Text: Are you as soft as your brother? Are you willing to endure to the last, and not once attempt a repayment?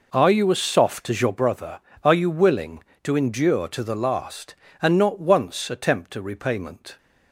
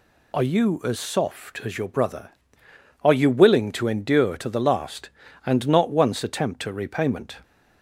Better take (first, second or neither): second